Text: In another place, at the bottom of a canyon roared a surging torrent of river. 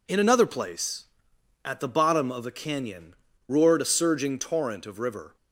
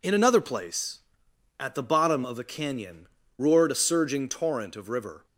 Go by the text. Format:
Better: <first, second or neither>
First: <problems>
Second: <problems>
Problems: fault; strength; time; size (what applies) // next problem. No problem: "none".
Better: neither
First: pauses between "canyon" and "roared"; slight; at 3.1 s; 0.32 s long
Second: pauses between "canyon" and "roared"; slight; at 3.0 s; 0.30 s long